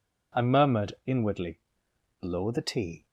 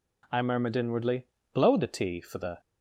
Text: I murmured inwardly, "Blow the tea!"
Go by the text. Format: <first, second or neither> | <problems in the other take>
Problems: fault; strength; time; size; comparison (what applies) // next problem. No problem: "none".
first | goes on to say "for the"; slight; from 2.2 s on; 0.38 s long